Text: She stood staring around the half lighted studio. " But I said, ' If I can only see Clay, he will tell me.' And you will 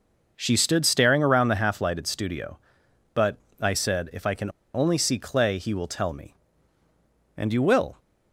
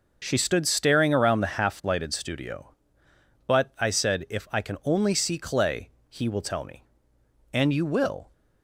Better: second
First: pauses between "But" and "I"; slight; at 3.3 s; 0.20 s long // pauses between "can" and "only"; slight; at 4.4 s; 0.24 s long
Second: none

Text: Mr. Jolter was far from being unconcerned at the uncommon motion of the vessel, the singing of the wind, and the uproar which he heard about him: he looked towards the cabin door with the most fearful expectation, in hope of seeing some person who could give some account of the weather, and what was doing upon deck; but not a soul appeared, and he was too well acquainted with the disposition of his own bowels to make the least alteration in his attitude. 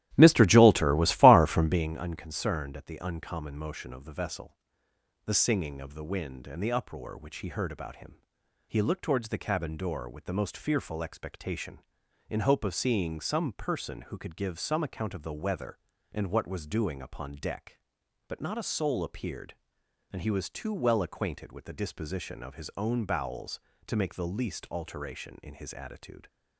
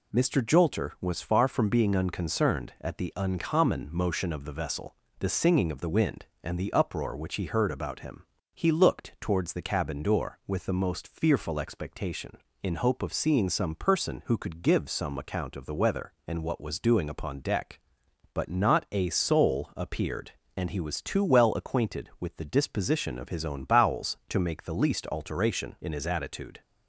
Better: second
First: starts louder than the rest; strong; until 2.0 s; 13 dB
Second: none

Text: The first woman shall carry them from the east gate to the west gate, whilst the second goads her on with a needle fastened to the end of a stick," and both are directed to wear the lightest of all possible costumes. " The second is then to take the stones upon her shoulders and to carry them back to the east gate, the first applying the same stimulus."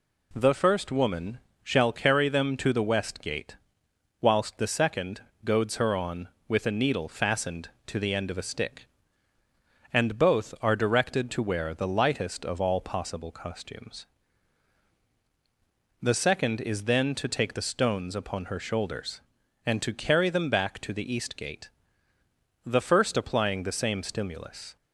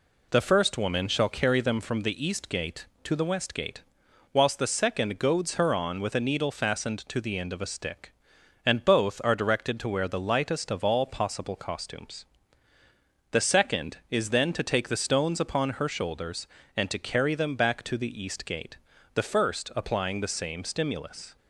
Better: second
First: pauses between "woman" and "shall"; slight; at 1.3 s; 0.22 s long // skips "from the east gate"; at 2.5 s // pauses between "second" and "goads"; slight; at 5.1 s; 0.24 s long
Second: none

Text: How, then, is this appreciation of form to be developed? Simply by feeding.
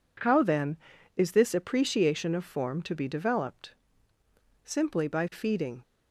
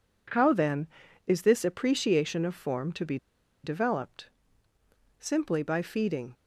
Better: first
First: none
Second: pauses between "be" and "developed"; noticeable; at 3.1 s; 0.47 s long

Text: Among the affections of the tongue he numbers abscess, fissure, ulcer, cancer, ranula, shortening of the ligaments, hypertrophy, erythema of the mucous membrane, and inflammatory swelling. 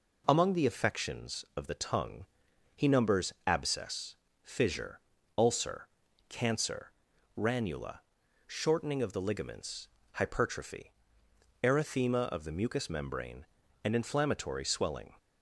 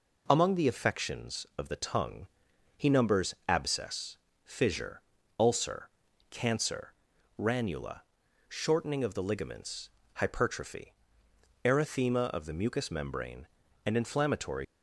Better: first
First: pauses between "tongue" and "he"; noticeable; at 2.2 s; 0.50 s long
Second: pauses between "tongue" and "he"; noticeable; at 2.2 s; 0.50 s long // stops before "swelling"; at 14.6 s

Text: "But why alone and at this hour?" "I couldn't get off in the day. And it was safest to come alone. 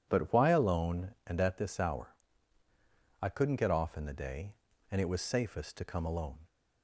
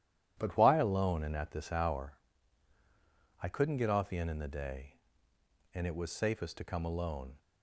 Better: first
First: none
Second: says "in" twice; at 4.2 s

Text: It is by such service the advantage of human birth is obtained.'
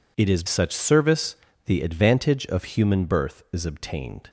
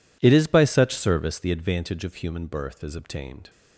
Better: second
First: skips "by"; at 0.4 s // pauses between "service" and "the"; slight; at 1.3 s; 0.30 s long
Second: none

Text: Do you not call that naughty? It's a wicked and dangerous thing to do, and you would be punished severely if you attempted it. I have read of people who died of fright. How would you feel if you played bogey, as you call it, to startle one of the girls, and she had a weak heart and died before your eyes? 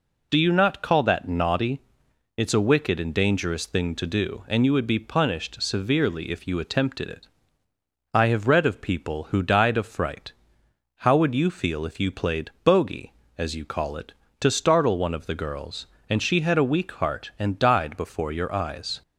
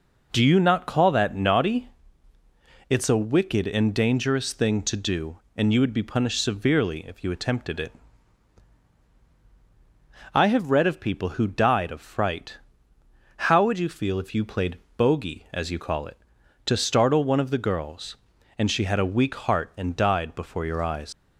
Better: first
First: none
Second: pauses between "played" and "bogey"; slight; at 14.7 s; 0.18 s long // leaves "eyes" unfinished; at 21.1 s; 115 ms

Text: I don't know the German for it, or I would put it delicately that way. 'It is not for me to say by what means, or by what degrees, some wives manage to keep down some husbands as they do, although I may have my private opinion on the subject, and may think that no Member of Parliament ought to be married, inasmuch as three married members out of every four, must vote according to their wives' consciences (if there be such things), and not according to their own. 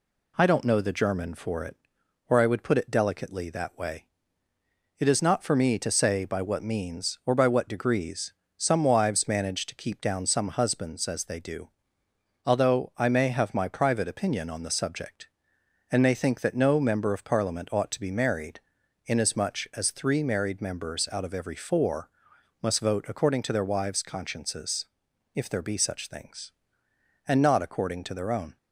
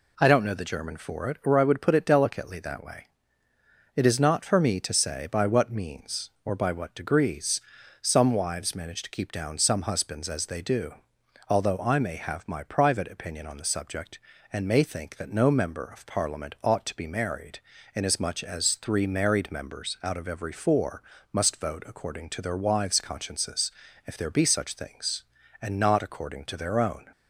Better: neither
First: none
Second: none

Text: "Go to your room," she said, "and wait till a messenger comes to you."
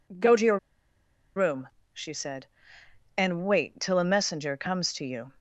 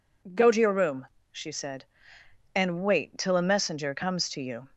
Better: second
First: pauses between "your" and "room"; noticeable; at 0.5 s; 0.79 s long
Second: none

